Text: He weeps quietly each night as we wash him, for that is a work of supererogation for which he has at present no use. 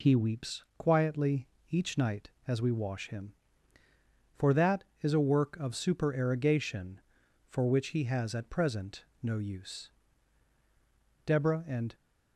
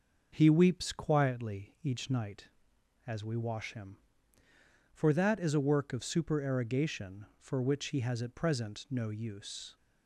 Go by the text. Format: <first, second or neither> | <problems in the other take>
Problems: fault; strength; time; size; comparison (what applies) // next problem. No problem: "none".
second | pauses between "weeps" and "quietly"; slight; at 0.6 s; 0.16 s long // pauses between "quietly" and "each"; slight; at 1.4 s; 0.22 s long // pauses between "present" and "no"; slight; at 9.0 s; 0.16 s long // goes on to say "Deborah and"; noticeable; from 11.2 s on; 0.66 s long